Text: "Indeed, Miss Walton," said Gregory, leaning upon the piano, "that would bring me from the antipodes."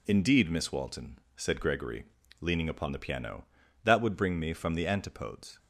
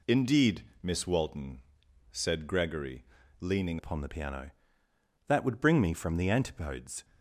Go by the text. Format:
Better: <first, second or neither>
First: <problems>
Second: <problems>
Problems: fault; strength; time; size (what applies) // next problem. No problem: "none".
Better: first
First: none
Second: changes voice at "upon"; from 3.7 s on; 3.3 s long